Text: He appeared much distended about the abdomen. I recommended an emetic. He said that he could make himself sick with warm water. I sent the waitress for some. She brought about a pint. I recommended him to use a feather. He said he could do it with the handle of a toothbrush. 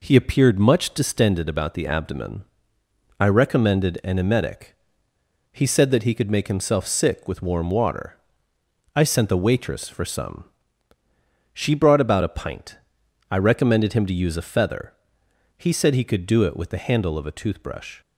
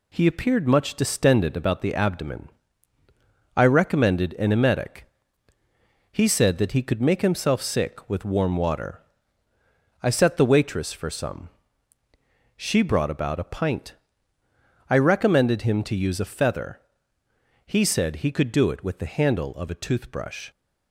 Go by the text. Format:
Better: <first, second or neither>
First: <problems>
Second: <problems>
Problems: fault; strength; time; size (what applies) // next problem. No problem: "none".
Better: first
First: none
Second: says "set" for "sent"; at 10.1 s